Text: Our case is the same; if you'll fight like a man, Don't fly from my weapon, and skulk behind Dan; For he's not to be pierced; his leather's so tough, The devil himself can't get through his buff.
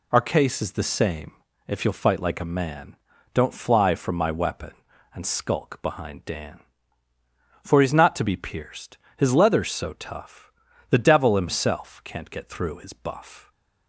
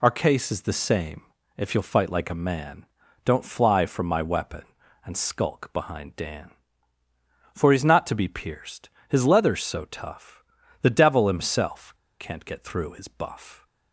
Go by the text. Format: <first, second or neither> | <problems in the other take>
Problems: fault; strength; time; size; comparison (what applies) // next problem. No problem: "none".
first | pauses between "himself" and "can't"; slight; at 11.9 s; 0.25 s long